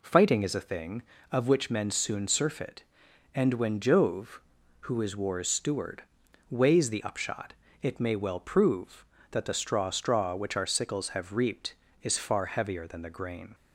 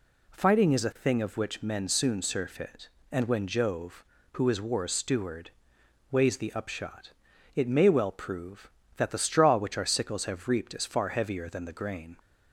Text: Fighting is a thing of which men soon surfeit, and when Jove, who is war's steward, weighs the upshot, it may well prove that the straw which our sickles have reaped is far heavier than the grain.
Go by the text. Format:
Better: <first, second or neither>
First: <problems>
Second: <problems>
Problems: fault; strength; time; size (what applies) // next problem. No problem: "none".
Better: second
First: says "straw" twice; at 9.9 s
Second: none